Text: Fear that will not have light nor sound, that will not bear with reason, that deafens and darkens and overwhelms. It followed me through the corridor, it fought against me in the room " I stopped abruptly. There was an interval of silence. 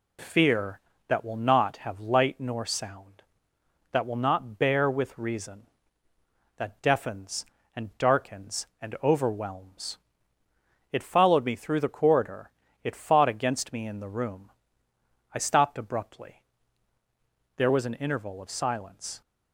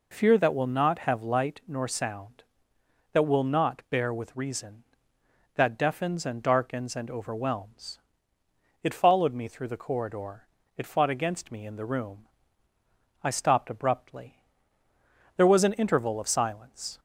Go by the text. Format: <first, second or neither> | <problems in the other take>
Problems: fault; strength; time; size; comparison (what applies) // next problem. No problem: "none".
neither | none